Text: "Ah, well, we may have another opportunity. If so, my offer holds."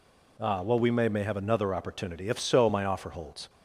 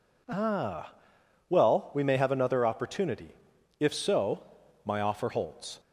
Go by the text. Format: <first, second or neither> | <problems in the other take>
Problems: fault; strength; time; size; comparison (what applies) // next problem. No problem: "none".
second | says "may" twice; at 1.0 s